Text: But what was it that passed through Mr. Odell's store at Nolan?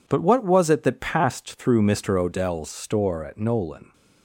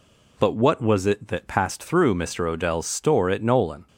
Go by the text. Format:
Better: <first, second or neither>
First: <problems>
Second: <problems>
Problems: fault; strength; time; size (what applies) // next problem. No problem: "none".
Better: neither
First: none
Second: none